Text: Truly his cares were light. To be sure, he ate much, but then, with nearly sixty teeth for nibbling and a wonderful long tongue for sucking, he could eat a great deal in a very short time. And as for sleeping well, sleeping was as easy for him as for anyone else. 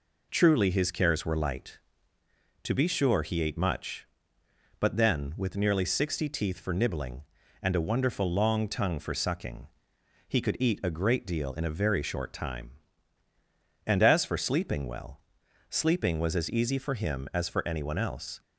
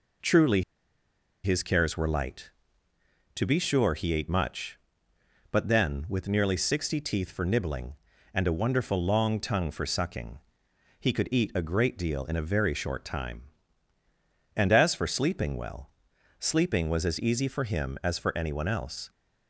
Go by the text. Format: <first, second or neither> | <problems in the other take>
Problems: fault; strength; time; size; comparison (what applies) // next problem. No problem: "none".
first | pauses between "Truly" and "his"; noticeable; at 0.6 s; 0.82 s long